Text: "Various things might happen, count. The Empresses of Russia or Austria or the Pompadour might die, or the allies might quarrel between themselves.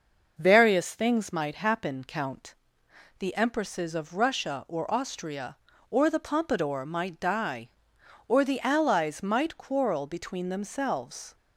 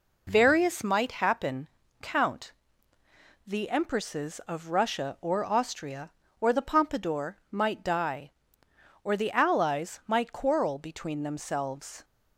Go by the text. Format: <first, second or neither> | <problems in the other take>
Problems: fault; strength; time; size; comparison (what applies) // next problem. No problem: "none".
first | skips "things"; at 0.8 s